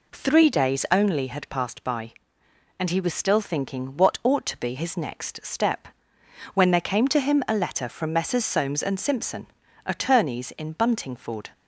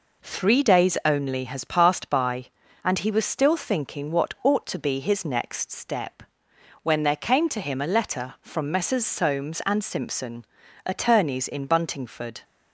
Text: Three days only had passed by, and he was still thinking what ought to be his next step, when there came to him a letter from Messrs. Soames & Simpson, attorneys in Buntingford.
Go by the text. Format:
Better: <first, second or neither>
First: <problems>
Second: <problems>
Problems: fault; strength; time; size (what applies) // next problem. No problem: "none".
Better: first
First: none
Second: says "has" for "had"; at 1.4 s